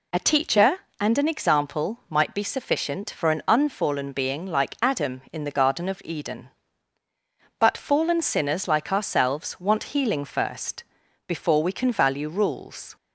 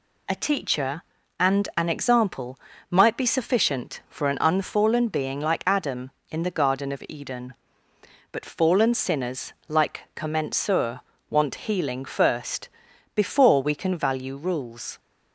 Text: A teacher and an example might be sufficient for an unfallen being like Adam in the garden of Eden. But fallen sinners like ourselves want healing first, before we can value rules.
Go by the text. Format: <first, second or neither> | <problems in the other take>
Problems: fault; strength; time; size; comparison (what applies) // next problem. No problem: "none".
first | pauses between "example" and "might"; slight; at 2.5 s; 0.32 s long // pauses between "sinners" and "like"; slight; at 9.5 s; 0.16 s long // says "commensur" for "ourselves"; at 10.1 s